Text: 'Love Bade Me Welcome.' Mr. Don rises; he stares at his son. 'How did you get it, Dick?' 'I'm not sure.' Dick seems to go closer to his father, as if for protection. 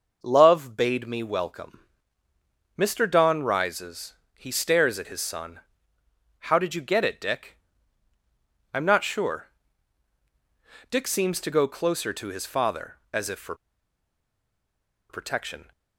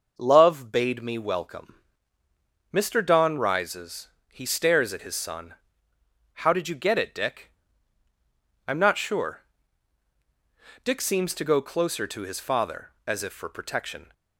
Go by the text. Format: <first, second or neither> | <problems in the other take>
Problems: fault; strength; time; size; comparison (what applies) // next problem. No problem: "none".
second | pauses between "for" and "protection"; strong; at 13.5 s; 1.5 s long